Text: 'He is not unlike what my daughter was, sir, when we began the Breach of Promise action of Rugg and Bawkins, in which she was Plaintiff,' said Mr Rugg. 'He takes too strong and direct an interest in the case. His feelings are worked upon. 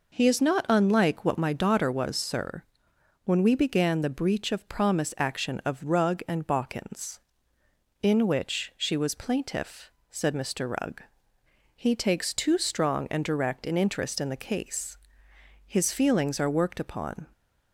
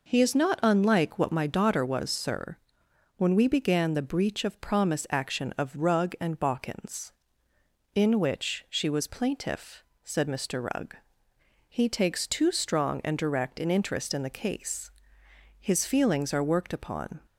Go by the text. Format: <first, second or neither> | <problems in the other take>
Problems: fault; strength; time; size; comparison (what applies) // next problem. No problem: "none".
neither | none